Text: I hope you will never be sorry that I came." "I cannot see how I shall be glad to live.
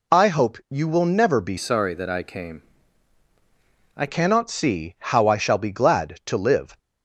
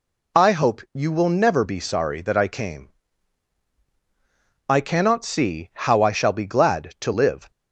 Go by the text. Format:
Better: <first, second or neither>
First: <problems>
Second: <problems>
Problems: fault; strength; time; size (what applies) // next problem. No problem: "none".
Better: second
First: changes voice from "sorry" to "I"; from 1.5 to 4.0 s; 2.5 s long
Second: none